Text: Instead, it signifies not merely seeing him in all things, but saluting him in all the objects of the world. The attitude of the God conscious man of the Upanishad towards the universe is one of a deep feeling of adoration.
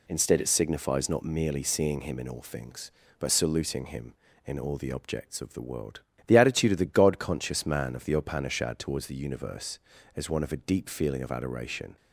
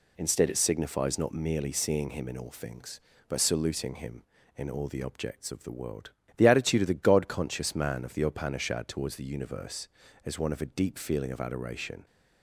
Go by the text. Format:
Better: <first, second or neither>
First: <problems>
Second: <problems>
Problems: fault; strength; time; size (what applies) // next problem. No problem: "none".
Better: neither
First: none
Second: none